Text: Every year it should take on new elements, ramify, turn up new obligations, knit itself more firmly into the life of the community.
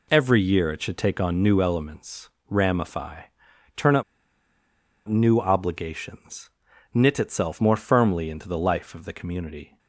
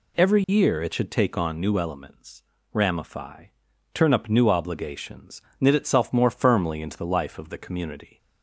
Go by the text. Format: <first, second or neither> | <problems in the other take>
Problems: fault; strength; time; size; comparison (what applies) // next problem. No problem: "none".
second | pauses between "up" and "new"; at 4.0 s; 1.0 s long